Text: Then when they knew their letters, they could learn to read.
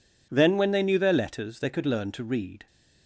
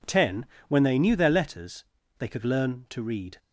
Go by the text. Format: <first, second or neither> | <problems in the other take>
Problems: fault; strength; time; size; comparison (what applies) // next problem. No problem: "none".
first | says "Ten" for "Then"; at 0.0 s